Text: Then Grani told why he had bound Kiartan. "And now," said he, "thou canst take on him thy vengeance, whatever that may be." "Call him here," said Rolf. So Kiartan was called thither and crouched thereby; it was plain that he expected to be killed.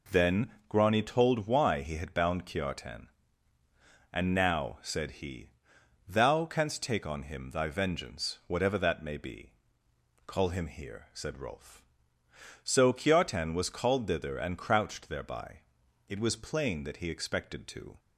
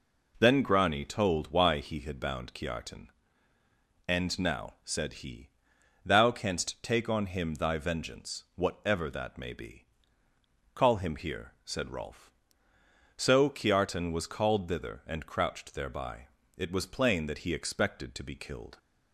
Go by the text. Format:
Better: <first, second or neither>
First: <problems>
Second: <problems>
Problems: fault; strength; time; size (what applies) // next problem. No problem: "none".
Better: second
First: pauses between "Then" and "Grani"; slight; at 0.4 s; 0.20 s long // stops before "be killed"; at 17.9 s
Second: none